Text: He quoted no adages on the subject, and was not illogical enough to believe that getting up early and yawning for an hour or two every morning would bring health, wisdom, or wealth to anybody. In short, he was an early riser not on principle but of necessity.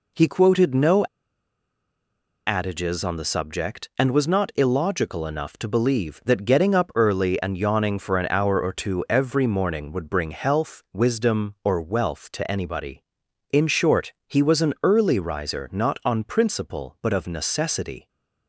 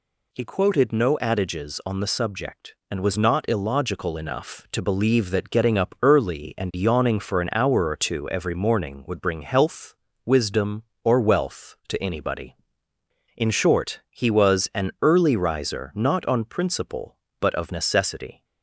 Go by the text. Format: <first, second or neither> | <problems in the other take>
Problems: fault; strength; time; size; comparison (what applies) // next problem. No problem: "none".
second | pauses between "no" and "adages"; strong; at 1.0 s; 1.4 s long